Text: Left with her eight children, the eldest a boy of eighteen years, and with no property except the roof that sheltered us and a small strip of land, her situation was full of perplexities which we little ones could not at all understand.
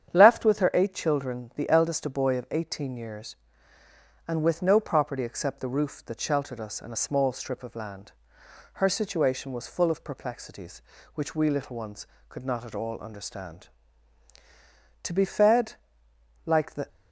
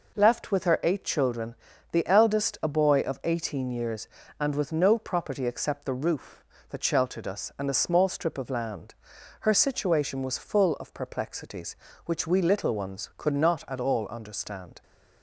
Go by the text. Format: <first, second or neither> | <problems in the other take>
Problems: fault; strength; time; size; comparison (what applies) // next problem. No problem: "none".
second | starts louder than the rest; strong; until 1.1 s; 9 dB // goes on to say "To be fed like the"; strong; from 15.0 s on; 1.8 s long